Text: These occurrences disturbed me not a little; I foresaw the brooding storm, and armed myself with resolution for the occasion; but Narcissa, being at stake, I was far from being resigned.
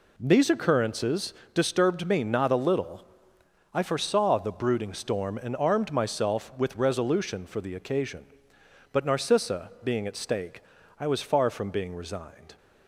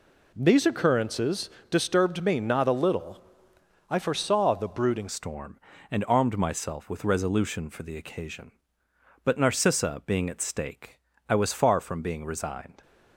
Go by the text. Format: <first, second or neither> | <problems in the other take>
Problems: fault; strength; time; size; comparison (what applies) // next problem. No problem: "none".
first | pauses between "occurrences" and "disturbed"; slight; at 1.4 s; 0.22 s long; slight in the first // changes voice at "storm"; from 5.0 s on; 7.8 s long